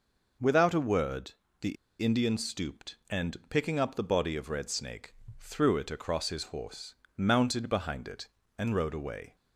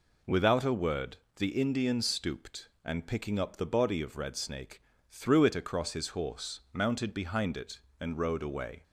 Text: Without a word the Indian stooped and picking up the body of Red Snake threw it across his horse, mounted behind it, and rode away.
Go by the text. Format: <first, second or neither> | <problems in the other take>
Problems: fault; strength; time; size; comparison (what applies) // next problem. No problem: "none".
second | pauses between "word" and "the"; slight; at 1.3 s; 0.26 s long; slight in the second // pauses between "the" and "Indian"; slight; at 1.7 s; 0.25 s long // pauses between "Snake" and "threw"; slight; at 5.1 s; 0.28 s long; slight in the second